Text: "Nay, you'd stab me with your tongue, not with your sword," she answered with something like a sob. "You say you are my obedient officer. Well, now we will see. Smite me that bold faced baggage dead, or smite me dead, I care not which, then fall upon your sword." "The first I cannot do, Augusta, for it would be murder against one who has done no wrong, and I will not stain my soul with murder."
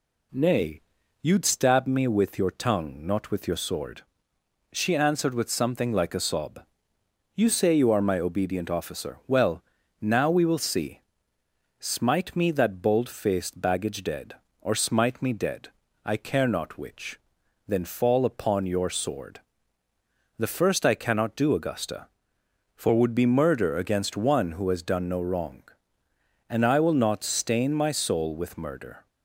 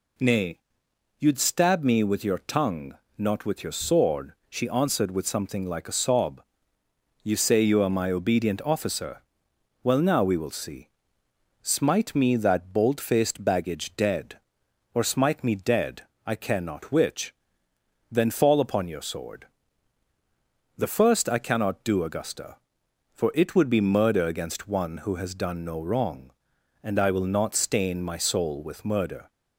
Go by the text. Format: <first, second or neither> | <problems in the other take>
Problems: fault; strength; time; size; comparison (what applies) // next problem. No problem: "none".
second | skips "it"; at 22.9 s